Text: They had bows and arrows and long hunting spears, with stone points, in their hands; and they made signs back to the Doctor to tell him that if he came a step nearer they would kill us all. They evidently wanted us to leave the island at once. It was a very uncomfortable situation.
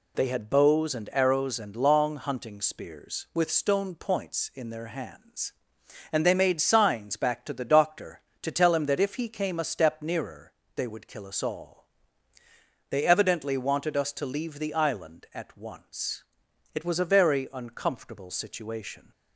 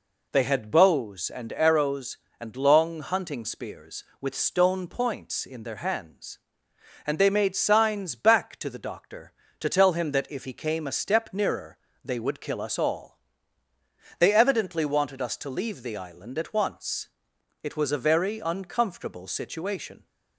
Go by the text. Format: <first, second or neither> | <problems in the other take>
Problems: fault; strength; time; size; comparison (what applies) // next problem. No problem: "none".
neither | pauses between "nearer" and "they"; slight; the same in both